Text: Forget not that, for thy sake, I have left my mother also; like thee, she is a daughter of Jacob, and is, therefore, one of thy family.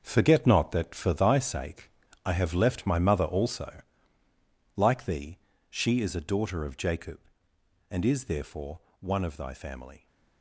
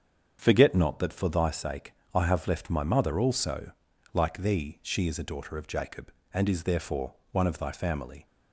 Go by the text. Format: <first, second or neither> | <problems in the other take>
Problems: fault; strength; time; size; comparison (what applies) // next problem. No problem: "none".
second | gets quieter; strong; throughout; 10 dB // starts louder than the rest; until 1.0 s; 6.5 dB; strong in the second